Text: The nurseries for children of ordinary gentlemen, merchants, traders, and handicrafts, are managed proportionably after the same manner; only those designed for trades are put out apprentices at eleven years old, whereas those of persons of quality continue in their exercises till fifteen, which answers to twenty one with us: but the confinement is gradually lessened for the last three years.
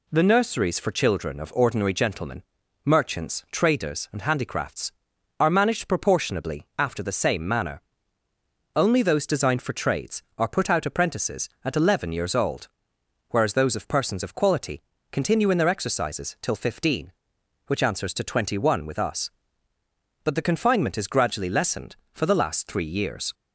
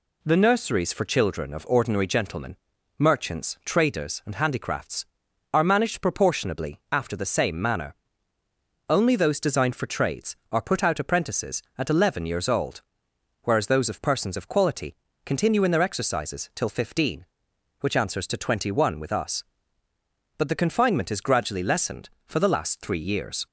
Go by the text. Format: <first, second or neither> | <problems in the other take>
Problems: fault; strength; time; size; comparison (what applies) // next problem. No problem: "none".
neither | pauses between "quality" and "continue"; slight; the same in both